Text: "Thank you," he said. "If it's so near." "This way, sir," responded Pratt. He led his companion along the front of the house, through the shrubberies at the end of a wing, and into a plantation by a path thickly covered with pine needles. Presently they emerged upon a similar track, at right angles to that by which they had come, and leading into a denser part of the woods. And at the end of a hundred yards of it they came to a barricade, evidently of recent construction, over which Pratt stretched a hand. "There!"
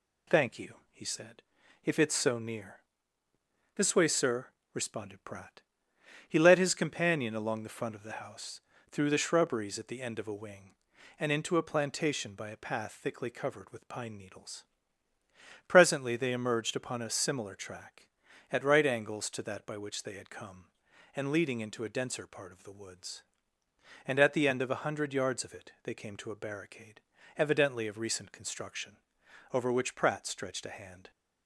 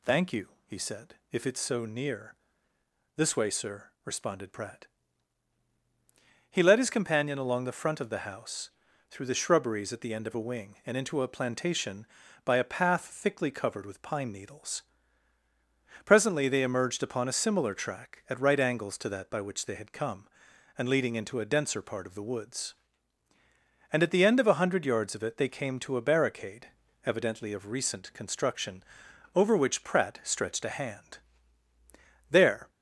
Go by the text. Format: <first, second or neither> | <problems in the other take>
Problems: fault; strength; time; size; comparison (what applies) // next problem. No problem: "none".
second | stops before "There"; at 31.1 s